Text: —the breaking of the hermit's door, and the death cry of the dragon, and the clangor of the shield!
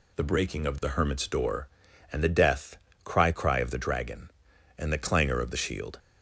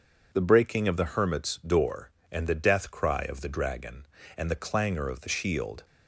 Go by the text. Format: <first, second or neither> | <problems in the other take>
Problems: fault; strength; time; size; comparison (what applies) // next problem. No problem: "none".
second | pauses between "death" and "cry"; slight; at 2.7 s; 0.28 s long // says "cry" twice; at 3.3 s